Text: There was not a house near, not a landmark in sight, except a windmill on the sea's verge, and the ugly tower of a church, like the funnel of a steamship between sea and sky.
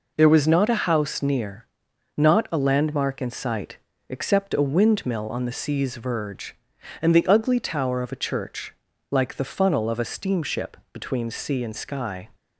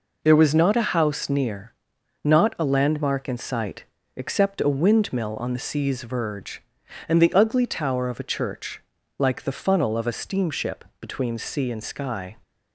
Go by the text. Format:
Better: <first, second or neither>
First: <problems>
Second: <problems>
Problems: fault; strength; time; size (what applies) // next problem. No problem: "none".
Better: neither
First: pauses between "steamship" and "between"; slight; at 10.7 s; 0.16 s long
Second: pauses between "steamship" and "between"; slight; at 10.8 s; 0.16 s long